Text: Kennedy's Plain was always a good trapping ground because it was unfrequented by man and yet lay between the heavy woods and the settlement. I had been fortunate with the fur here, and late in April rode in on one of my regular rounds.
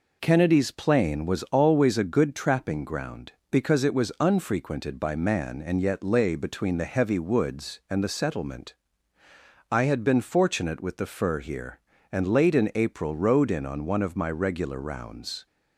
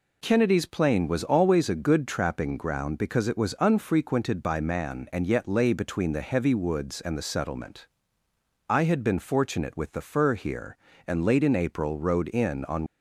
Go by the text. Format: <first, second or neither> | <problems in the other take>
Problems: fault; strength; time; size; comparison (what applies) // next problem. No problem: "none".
first | stops before "one of my regular rounds"; at 12.8 s